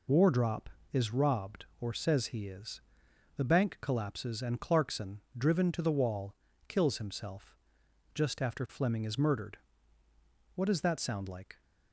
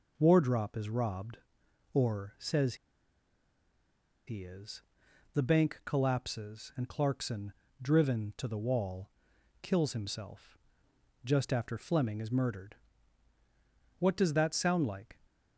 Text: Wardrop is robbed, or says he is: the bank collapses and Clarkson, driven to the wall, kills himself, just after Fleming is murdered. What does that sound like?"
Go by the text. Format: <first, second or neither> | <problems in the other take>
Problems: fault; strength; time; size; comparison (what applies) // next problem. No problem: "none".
first | pauses between "says" and "he"; strong; at 2.7 s; 1.5 s long